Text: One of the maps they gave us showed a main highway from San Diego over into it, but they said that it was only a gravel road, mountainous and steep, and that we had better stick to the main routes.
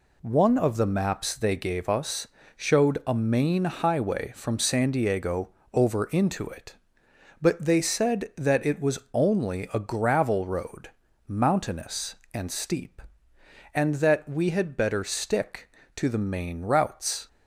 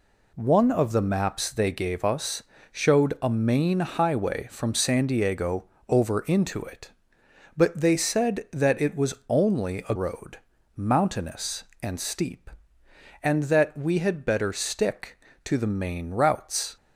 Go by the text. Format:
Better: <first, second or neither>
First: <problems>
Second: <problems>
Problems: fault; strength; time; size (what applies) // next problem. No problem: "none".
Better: first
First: pauses between "us" and "showed"; slight; at 2.2 s; 0.30 s long // pauses between "Diego" and "over"; slight; at 5.4 s; 0.22 s long // pauses between "was" and "only"; slight; at 8.9 s; 0.16 s long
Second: pauses between "us" and "showed"; slight; at 2.4 s; 0.30 s long // pauses between "Diego" and "over"; slight; at 5.6 s; 0.22 s long // pauses between "was" and "only"; slight; at 9.1 s; 0.16 s long // skips "gravel"; at 9.9 s